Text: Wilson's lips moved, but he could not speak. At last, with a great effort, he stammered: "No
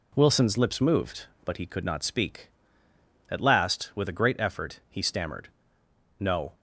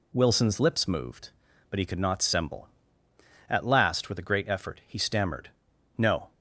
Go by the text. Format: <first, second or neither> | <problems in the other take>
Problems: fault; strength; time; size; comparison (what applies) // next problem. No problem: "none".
first | says "semble" for "speak"; at 2.2 s